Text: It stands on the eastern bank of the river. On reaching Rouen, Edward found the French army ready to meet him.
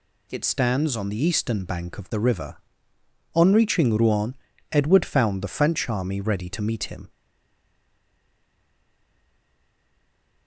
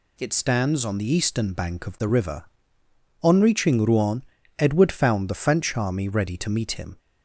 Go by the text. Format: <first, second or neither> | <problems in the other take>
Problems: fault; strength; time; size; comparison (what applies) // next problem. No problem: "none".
second | stays silent after the last word; strong; from 7.0 s on; 3.4 s long